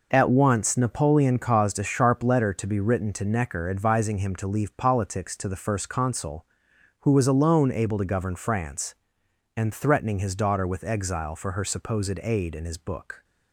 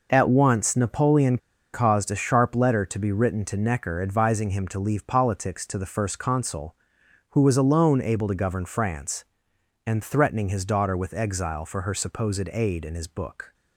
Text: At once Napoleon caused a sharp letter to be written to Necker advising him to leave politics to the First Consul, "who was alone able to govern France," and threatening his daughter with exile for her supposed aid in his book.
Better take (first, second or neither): first